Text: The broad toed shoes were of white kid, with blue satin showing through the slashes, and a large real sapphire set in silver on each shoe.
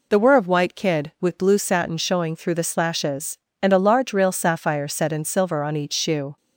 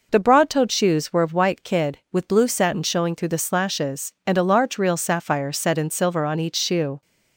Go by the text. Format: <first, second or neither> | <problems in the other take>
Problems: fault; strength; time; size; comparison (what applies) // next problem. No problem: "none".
second | skips "broad toed shoes"; at 0.1 s